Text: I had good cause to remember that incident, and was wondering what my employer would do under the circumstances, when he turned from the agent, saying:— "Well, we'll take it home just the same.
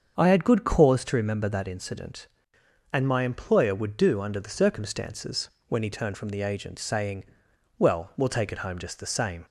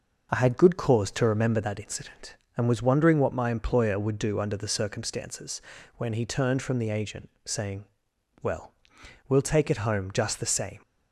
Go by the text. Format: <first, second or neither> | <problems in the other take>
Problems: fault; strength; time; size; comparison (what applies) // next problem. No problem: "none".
second | starts louder than the rest; until 1.1 s; 7 dB // skips "was wondering what"; at 3.0 s